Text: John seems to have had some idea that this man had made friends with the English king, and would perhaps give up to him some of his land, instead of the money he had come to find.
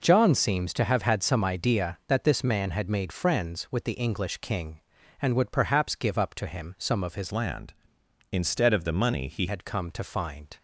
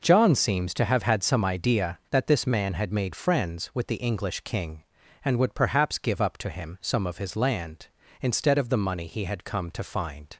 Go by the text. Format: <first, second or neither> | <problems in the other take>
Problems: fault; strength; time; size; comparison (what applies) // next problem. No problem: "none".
second | changes voice from "land" to "he"; from 7.3 to 9.4 s; 2.1 s long